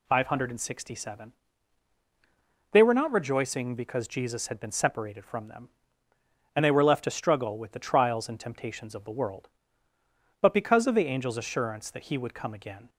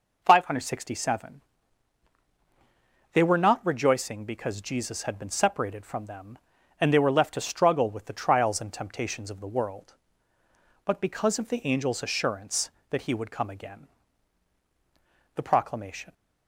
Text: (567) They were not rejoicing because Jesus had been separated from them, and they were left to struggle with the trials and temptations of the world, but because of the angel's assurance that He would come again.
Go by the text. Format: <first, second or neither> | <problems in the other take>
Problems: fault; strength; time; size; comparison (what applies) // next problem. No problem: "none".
first | goes on to say "The proclamation"; noticeable; from 15.3 s on; 0.76 s long